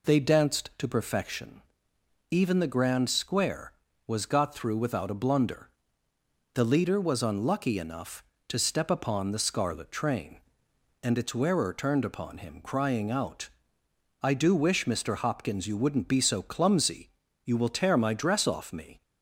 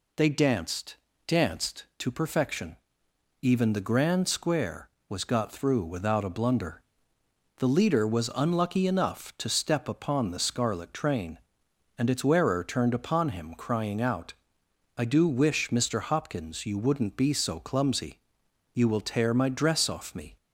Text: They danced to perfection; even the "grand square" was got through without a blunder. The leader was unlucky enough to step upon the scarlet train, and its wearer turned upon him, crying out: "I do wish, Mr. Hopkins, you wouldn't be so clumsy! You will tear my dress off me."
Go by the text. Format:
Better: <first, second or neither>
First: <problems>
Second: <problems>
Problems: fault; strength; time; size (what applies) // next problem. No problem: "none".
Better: first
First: none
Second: says "danced" twice; at 1.2 s